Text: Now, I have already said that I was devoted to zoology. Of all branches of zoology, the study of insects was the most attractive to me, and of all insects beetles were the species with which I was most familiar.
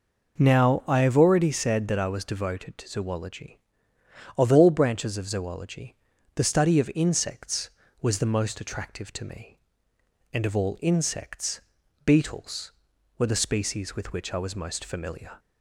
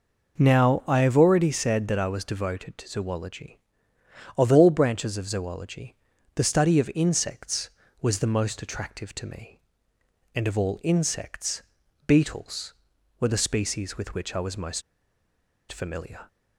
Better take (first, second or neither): first